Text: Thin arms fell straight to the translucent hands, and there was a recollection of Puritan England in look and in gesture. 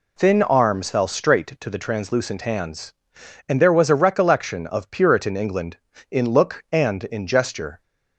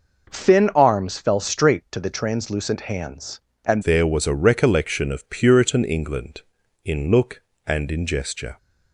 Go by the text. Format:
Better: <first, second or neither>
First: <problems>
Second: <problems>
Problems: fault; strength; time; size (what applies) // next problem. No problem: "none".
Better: first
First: none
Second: changes voice at "there"; from 3.8 s on; 4.7 s long